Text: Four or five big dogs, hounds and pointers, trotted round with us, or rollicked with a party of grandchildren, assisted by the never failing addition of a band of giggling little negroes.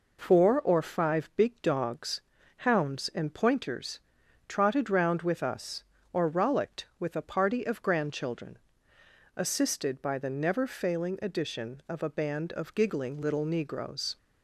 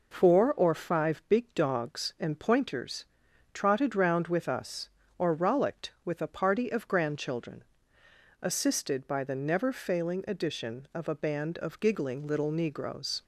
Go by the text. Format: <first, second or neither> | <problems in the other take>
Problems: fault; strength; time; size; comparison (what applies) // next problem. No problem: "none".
first | skips "hounds"; at 2.1 s